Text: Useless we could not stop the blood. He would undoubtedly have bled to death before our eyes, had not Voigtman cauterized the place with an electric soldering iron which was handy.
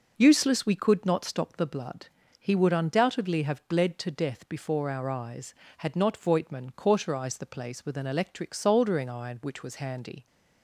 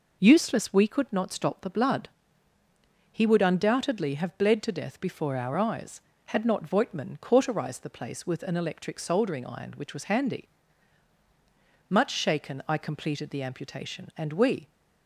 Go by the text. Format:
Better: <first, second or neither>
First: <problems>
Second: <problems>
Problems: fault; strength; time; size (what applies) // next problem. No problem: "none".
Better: first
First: none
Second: goes on to say "Much shaken I completed the amputation and we"; strong; from 11.8 s on; 2.8 s long